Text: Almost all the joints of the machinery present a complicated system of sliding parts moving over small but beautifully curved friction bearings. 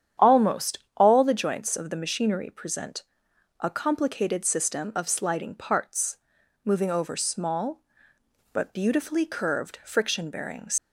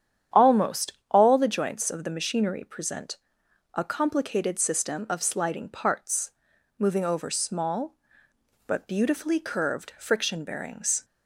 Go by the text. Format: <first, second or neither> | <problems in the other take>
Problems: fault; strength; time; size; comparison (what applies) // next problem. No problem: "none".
second | starts louder than the rest; strong; until 1.3 s; 9 dB; strong in the second // pauses between "Almost" and "all"; slight; at 0.7 s; 0.18 s long; slight in the second // pauses between "present" and "a"; noticeable; at 3.0 s; 0.56 s long; noticeable in the second // pauses between "parts" and "moving"; noticeable; at 6.1 s; 0.48 s long; noticeable in the second // leaves "bearings" unfinished; at 10.7 s; 125 ms